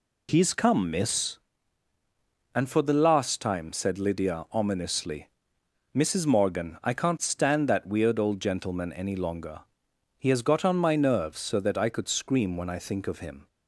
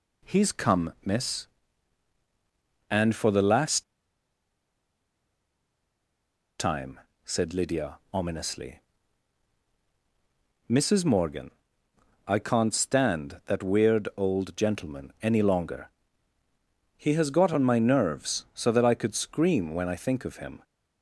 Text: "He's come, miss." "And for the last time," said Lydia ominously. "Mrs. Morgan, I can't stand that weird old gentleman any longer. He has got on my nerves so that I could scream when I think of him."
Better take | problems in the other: first | pauses between "last" and "time"; strong; at 3.8 s; 2.7 s long

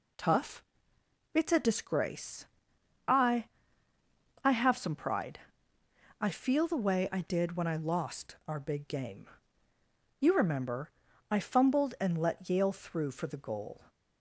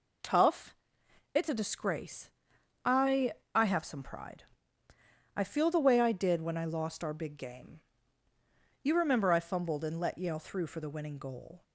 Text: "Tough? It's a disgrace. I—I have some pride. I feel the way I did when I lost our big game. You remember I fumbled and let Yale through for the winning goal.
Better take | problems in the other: second | pauses between "remember" and "I"; at 10.9 s; 0.38 s long // skips "winning"; at 13.3 s

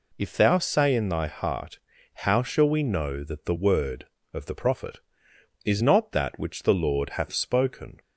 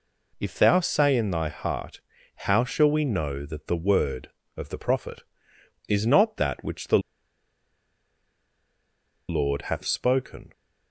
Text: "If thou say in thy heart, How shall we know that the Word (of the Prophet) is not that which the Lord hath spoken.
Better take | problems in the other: first | pauses between "the" and "Lord"; strong; at 6.9 s; 2.3 s long

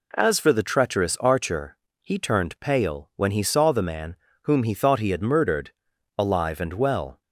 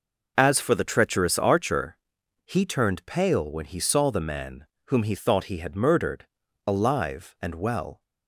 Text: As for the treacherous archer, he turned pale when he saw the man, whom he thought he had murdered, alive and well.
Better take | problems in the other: neither | none

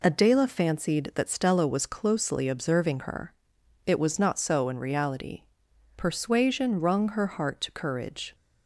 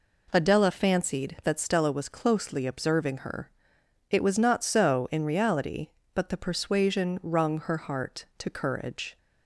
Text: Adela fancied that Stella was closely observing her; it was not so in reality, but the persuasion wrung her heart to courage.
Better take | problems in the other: second | skips "but the"; at 5.6 s

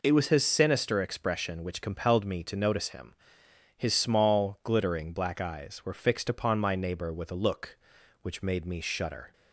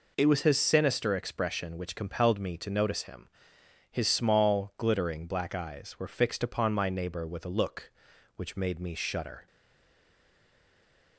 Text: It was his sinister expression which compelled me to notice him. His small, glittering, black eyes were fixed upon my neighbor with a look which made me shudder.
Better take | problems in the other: first | stays silent after the last word; noticeable; from 9.4 s on; 1.7 s long

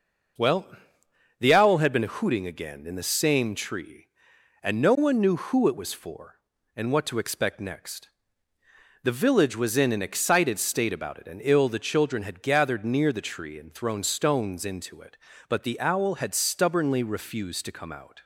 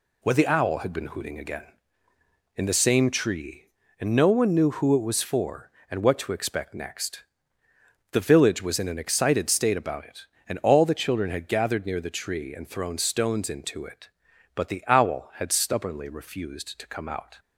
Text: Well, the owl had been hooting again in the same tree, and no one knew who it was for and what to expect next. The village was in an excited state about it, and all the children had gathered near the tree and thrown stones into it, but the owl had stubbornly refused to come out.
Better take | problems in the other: second | says "ill" for "all"; at 11.4 s

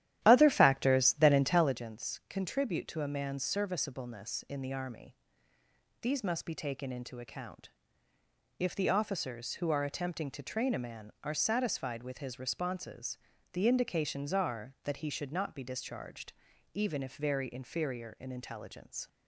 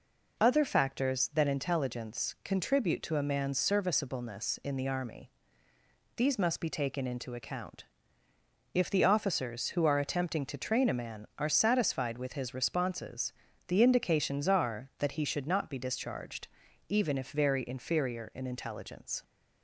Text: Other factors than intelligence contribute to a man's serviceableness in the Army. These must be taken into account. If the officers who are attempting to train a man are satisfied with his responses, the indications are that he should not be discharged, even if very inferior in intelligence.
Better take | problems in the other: second | starts louder than the rest; strong; until 1.9 s; 12.5 dB

